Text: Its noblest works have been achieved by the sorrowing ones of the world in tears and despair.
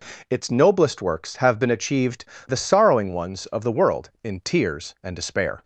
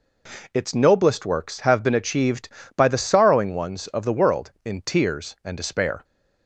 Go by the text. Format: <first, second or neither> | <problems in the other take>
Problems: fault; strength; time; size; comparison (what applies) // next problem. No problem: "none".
second | skips "by"; at 2.3 s